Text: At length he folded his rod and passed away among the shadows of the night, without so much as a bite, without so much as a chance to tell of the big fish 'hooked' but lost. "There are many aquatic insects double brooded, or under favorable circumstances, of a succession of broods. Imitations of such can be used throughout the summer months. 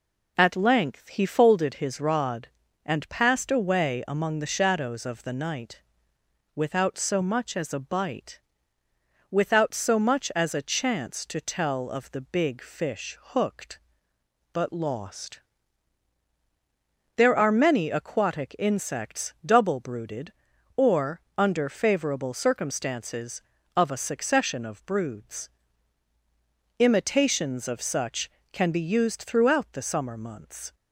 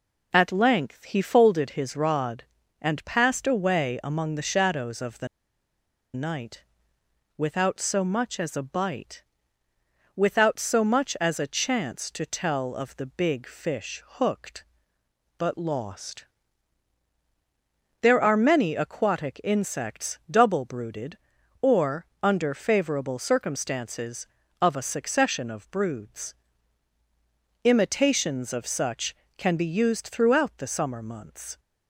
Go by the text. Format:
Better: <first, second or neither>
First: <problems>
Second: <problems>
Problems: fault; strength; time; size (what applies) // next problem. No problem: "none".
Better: first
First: pauses between "or" and "under"; slight; at 21.1 s; 0.16 s long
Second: pauses between "the" and "night"; noticeable; at 5.2 s; 0.87 s long // pauses between "or" and "under"; slight; at 22.0 s; 0.16 s long